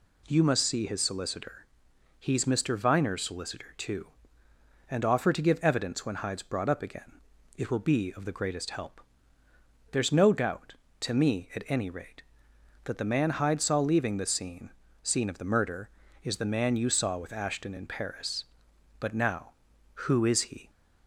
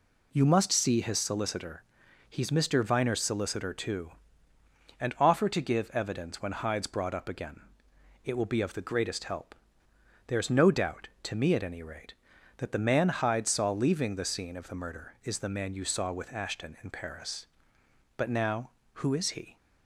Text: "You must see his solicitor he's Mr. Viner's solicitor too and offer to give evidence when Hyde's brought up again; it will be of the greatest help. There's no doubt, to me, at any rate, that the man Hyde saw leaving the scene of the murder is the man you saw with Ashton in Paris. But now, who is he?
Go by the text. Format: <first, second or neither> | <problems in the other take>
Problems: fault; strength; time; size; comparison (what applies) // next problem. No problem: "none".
second | pauses between "solicitor" and "he's"; noticeable; at 1.6 s; 0.52 s long; noticeable in the second // says "scene" twice; at 15.0 s